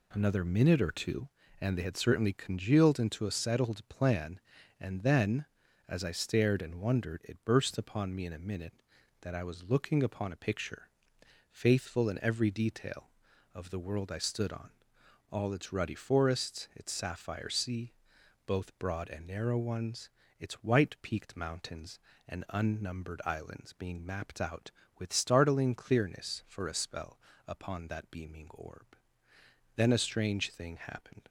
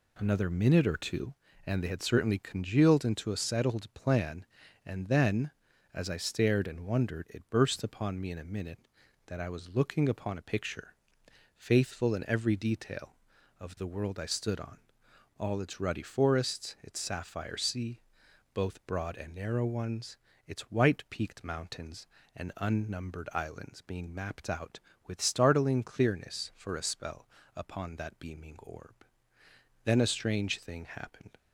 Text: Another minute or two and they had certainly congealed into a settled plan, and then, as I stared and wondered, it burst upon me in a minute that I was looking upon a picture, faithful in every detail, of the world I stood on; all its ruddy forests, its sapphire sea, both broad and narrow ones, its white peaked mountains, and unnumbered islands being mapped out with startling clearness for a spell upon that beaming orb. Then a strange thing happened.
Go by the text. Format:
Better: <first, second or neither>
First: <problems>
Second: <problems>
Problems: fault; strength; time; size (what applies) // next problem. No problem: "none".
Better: neither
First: pauses between "spell" and "upon"; slight; at 27.1 s; 0.28 s long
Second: pauses between "spell" and "upon"; slight; at 27.2 s; 0.28 s long